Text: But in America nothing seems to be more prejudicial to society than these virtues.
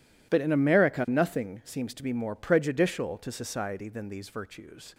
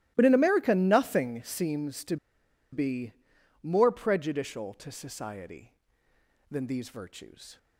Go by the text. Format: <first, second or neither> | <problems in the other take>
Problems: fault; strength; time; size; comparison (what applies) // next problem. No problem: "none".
first | starts louder than the rest; strong; until 1.1 s; 15.5 dB // pauses between "to" and "be"; noticeable; at 2.1 s; 0.56 s long // pauses between "be" and "more"; noticeable; at 3.1 s; 0.48 s long